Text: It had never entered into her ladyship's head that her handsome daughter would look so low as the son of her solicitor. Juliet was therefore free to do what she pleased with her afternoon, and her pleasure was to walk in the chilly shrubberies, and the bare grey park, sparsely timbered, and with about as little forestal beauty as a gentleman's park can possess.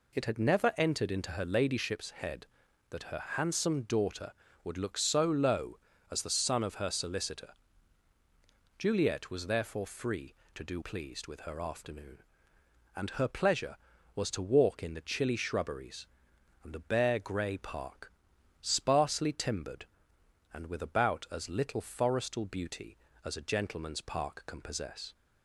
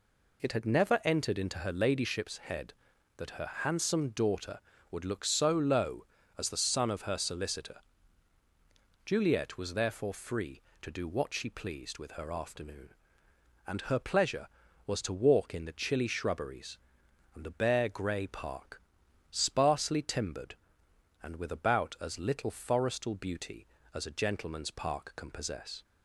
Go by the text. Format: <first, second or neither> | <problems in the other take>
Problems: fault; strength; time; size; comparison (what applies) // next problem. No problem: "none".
second | skips "what she"; at 10.8 s